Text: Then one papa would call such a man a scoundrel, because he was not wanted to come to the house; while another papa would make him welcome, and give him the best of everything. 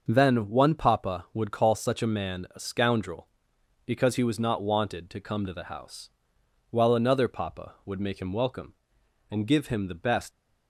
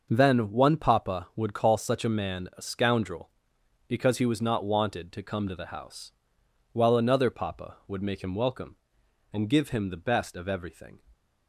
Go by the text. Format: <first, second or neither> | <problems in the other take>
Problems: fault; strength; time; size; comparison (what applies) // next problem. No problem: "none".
second | starts louder than the rest; until 1.0 s; 6.5 dB; also in the second // stops before "of everything"; at 10.3 s